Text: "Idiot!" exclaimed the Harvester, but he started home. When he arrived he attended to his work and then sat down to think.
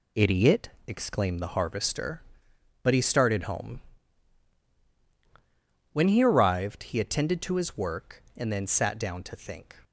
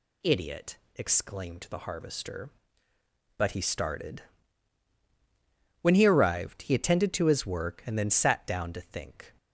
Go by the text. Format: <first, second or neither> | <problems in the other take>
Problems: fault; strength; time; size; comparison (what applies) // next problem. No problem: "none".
first | skips "home"; at 5.0 s